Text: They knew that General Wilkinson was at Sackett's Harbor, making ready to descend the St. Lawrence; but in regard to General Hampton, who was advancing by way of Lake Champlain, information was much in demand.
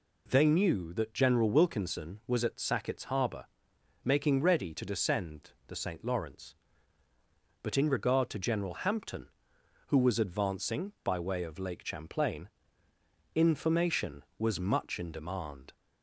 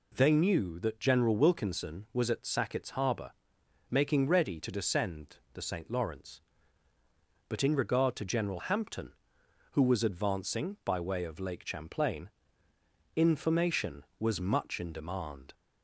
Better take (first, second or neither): neither